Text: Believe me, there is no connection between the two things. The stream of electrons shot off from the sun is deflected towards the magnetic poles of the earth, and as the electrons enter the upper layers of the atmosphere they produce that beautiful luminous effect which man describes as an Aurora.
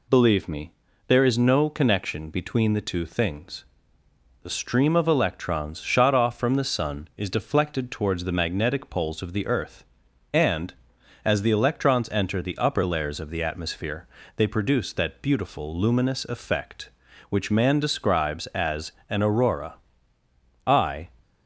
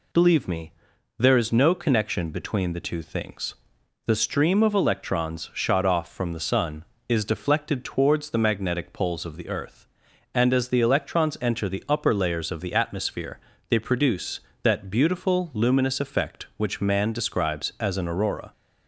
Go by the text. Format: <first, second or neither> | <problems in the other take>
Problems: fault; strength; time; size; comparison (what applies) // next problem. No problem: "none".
second | pauses between "atmosphere" and "they"; slight; at 14.0 s; 0.30 s long; slight in the second // pauses between "as" and "an"; slight; at 18.9 s; 0.16 s long // goes on to say "I"; slight; from 20.6 s on; 0.42 s long